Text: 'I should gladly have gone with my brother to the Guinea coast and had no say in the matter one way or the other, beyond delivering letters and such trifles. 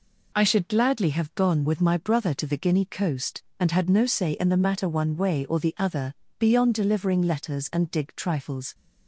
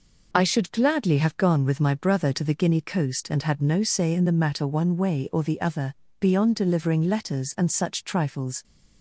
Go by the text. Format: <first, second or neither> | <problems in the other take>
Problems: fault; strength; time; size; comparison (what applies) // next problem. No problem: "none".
second | says "dig" for "such"; at 7.9 s